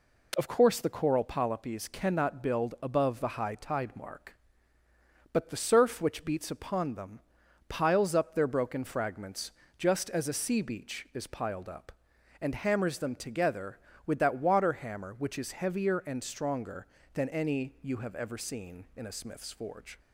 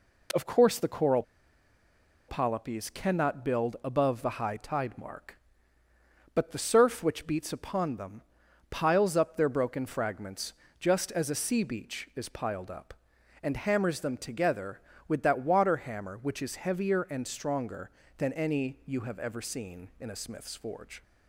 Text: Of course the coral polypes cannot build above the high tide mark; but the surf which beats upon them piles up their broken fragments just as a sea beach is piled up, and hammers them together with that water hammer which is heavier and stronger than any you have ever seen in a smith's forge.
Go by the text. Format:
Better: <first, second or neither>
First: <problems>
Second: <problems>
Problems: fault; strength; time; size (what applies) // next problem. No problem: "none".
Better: first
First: pauses between "them" and "piles"; noticeable; at 7.2 s; 0.48 s long // pauses between "fragments" and "just"; slight; at 9.5 s; 0.26 s long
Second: pauses between "coral" and "polypes"; at 1.2 s; 1.0 s long // pauses between "them" and "piles"; noticeable; at 8.2 s; 0.48 s long // pauses between "fragments" and "just"; slight; at 10.5 s; 0.26 s long